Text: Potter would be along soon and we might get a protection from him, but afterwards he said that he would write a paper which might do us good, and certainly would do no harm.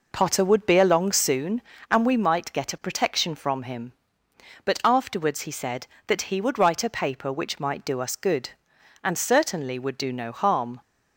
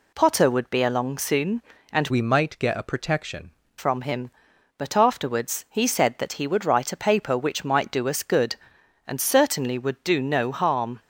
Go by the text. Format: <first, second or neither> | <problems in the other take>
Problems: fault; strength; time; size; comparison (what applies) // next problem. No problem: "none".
first | changes voice from "we" to "protection"; from 2.0 to 3.4 s; 1.4 s long